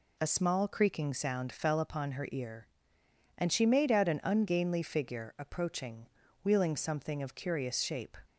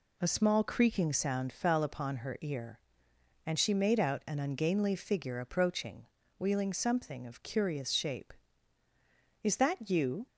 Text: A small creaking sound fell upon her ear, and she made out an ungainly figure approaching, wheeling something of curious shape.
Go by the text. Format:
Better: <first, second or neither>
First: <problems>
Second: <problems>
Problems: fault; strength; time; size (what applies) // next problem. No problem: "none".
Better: first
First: none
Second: goes on to say "Is that you"; noticeable; from 9.4 s on; 0.82 s long